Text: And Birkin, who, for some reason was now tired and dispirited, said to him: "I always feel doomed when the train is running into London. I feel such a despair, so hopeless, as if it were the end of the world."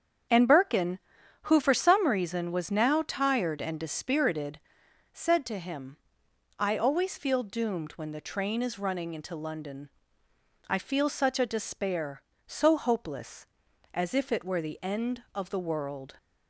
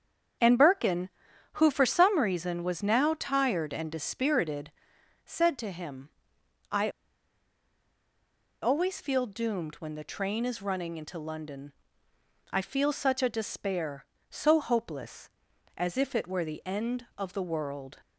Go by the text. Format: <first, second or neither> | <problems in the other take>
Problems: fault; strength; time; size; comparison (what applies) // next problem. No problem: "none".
first | starts louder than the rest; strong; until 1.8 s; 8 dB; strong in the first // pauses between "I" and "always"; strong; at 6.9 s; 1.7 s long